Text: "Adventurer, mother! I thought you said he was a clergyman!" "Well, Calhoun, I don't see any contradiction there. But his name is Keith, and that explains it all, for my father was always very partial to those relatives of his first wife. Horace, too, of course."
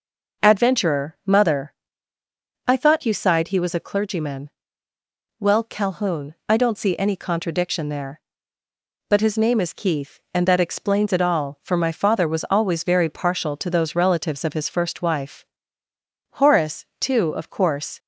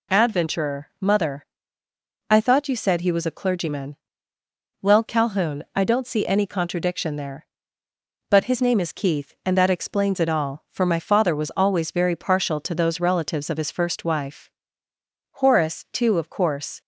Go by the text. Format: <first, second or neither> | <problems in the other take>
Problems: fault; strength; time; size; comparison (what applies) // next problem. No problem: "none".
second | says "sighed" for "said"; at 3.1 s